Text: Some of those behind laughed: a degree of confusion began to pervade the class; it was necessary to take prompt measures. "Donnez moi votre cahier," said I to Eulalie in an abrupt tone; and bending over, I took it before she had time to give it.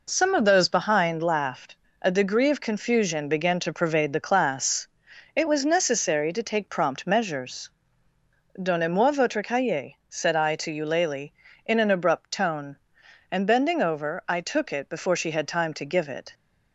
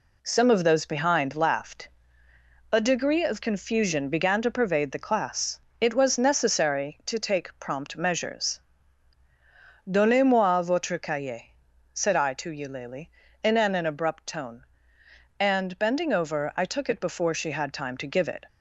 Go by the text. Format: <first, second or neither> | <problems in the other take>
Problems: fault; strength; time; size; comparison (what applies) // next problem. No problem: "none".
first | says "an" twice; at 13.7 s